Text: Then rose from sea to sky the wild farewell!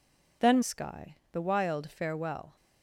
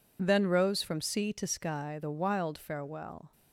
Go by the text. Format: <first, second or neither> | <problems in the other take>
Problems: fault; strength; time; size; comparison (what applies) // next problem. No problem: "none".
second | skips "rose from sea to"; at 0.6 s // pauses between "sky" and "the"; slight; at 1.1 s; 0.16 s long